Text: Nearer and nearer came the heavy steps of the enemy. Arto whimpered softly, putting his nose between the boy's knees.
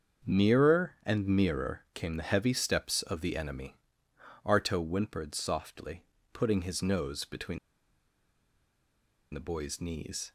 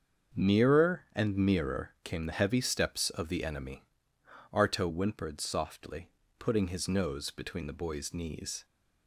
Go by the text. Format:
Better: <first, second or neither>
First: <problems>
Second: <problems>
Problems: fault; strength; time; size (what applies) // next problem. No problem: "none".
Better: second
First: starts louder than the rest; until 1.3 s; 7 dB // pauses between "between" and "the"; strong; at 7.5 s; 1.7 s long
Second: starts louder than the rest; until 1.4 s; 7 dB